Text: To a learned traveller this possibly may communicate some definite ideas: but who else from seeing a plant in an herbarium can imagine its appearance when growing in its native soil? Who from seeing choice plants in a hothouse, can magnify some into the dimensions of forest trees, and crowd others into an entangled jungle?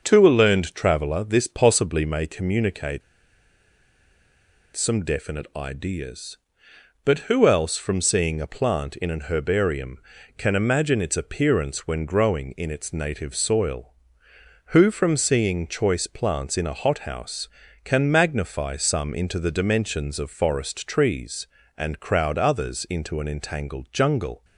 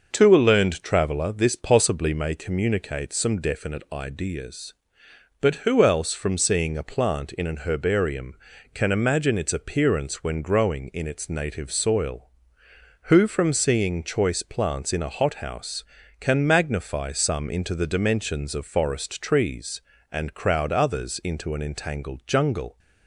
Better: second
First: pauses between "communicate" and "some"; strong; at 3.0 s; 1.7 s long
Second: none

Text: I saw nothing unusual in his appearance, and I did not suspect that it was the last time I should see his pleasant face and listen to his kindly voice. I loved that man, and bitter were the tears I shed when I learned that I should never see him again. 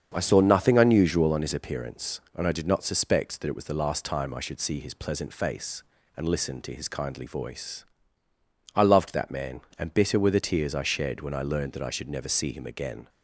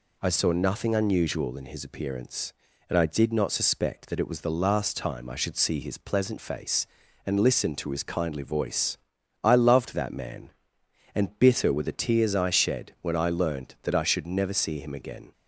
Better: second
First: starts louder than the rest; strong; until 1.1 s; 7.5 dB // says "on" for "in"; at 1.3 s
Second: none

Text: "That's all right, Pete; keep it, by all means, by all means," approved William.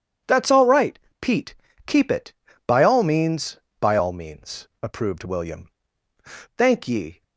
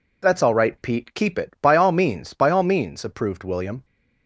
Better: second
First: goes on to say "Thank ye"; noticeable; from 6.5 s on; 0.66 s long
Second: none

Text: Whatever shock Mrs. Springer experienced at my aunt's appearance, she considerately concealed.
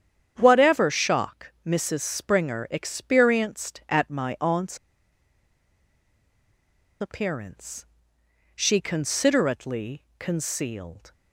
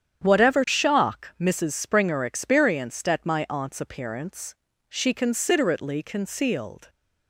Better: second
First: starts louder than the rest; strong; until 1.3 s; 9 dB // pauses between "aunt's" and "appearance"; strong; at 4.7 s; 2.2 s long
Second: starts louder than the rest; strong; until 1.2 s; 9 dB

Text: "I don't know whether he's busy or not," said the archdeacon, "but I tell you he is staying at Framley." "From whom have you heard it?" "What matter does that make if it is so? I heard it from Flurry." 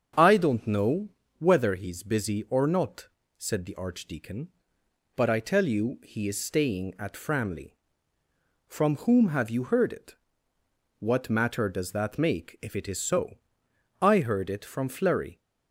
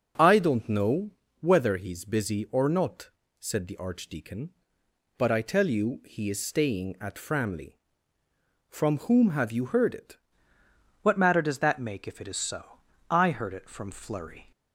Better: first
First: starts louder than the rest; strong; until 1.4 s; 7.5 dB // pauses between "know" and "whether"; slight; at 1.0 s; 0.32 s long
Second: starts louder than the rest; noticeable; until 1.4 s; 6 dB // pauses between "know" and "whether"; slight; at 1.1 s; 0.32 s long // changes voice at "What"; from 11.0 s on; 3.5 s long

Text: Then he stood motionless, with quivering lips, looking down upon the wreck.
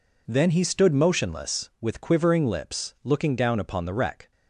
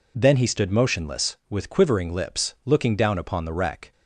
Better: neither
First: none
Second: none

